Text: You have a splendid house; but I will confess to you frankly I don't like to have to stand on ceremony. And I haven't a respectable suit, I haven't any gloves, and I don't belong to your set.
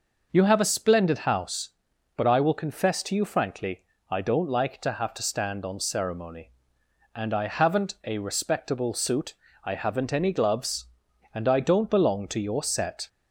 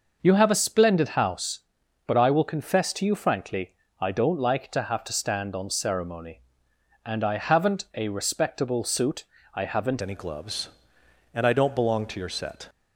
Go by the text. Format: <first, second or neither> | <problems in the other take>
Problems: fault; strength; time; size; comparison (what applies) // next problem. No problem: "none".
first | pauses between "frankly" and "I"; slight; at 3.7 s; 0.30 s long; slight in the first // changes voice at "any"; from 10.0 s on; 2.6 s long